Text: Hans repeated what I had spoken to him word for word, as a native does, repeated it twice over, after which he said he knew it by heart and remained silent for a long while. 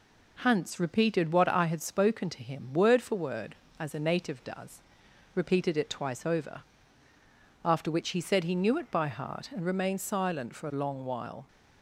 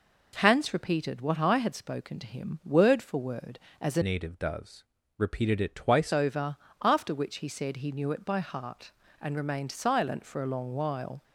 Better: first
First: none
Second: changes voice from "native" to "twice"; from 4.0 to 6.1 s; 2.1 s long

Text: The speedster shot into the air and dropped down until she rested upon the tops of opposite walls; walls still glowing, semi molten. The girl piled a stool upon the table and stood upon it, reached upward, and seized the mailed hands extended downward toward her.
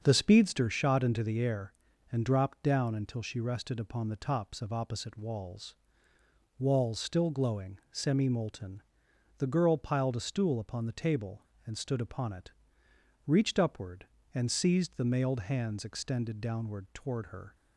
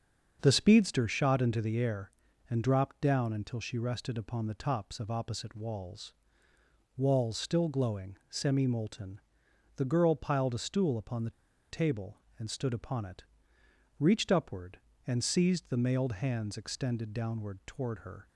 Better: first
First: starts louder than the rest; strong; until 1.0 s; 7 dB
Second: starts louder than the rest; until 1.4 s; 7 dB // pauses between "the" and "table"; at 11.3 s; 0.40 s long

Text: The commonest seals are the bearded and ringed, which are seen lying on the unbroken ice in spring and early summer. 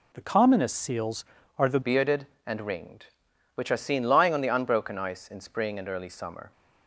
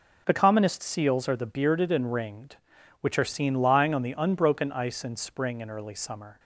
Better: second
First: changes voice at "bearded"; from 1.8 s on; 4.7 s long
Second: none

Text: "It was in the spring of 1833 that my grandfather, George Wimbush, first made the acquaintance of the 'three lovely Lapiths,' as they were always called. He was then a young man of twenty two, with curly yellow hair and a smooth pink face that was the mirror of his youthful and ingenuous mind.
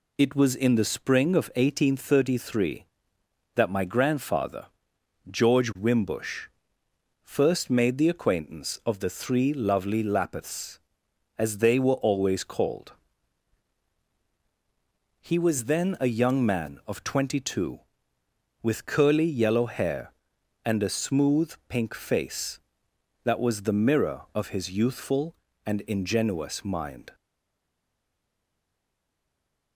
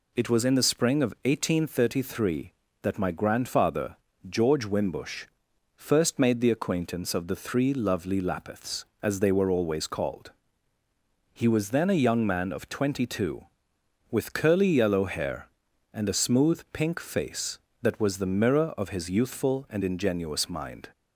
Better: second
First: stays silent after the last word; strong; from 27.1 s on; 2.6 s long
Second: none

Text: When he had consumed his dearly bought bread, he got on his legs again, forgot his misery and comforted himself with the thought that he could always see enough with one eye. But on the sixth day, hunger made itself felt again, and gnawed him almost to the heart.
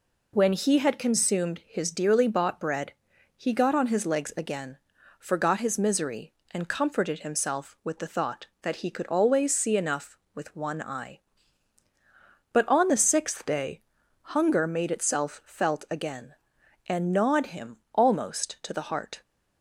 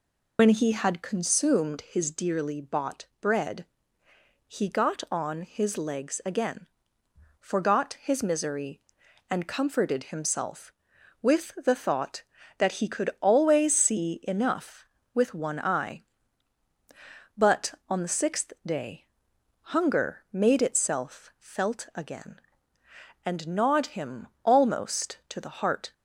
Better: first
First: pauses between "him" and "almost"; slight; at 17.7 s; 0.16 s long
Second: loses the start of "When"; at 0.3 s; 70 ms // pauses between "him" and "almost"; slight; at 24.2 s; 0.18 s long

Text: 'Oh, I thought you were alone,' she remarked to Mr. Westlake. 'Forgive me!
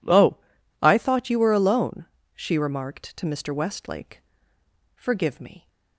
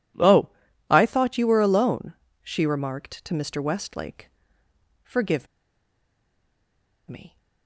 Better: first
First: none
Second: pauses between "Forgive" and "me"; strong; at 5.4 s; 1.6 s long

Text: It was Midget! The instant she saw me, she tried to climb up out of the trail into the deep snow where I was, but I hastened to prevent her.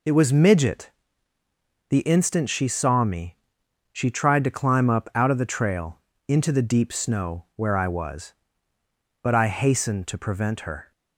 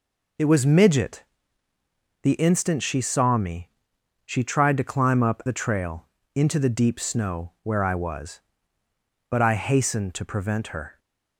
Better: first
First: pauses between "trail" and "into"; slight; at 5.9 s; 0.30 s long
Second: skips "out of"; at 5.4 s // pauses between "trail" and "into"; slight; at 6.0 s; 0.30 s long

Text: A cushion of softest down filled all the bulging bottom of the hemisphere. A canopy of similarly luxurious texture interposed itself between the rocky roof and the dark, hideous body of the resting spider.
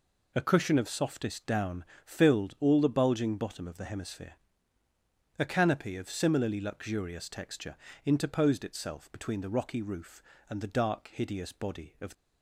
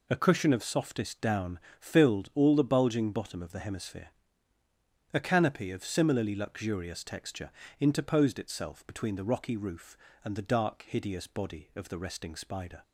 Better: second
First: pauses between "down" and "filled"; slight; at 1.8 s; 0.22 s long // pauses between "texture" and "interposed"; slight; at 7.7 s; 0.30 s long // stops before "the resting spider"; at 12.1 s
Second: pauses between "down" and "filled"; slight; at 1.5 s; 0.22 s long // pauses between "texture" and "interposed"; slight; at 7.4 s; 0.30 s long

